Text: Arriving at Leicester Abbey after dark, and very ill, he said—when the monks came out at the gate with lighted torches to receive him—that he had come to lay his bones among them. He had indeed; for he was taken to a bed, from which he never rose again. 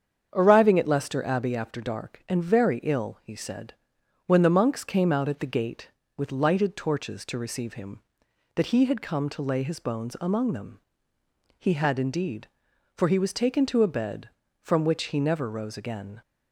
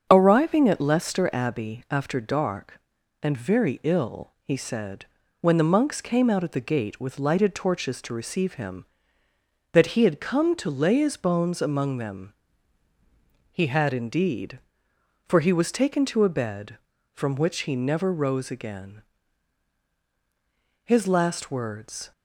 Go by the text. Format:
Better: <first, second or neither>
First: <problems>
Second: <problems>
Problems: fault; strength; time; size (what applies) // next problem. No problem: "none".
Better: first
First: starts louder than the rest; strong; until 1.3 s; 7.5 dB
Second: starts louder than the rest; until 1.1 s; 7 dB // goes on to say "His last words"; noticeable; from 20.8 s on; 1.2 s long